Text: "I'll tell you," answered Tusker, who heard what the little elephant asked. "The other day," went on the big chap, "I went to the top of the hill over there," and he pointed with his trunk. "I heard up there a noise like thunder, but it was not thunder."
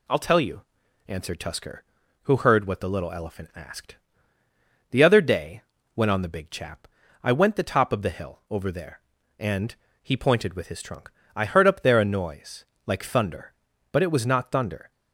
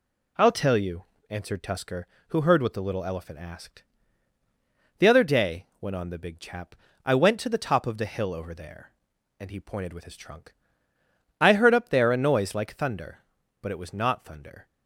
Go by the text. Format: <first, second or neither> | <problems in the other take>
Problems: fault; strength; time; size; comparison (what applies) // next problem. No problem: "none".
second | skips "to"; at 7.5 s // pauses between "and" and "he"; slight; at 9.7 s; 0.28 s long // pauses between "noise" and "like"; slight; at 12.6 s; 0.18 s long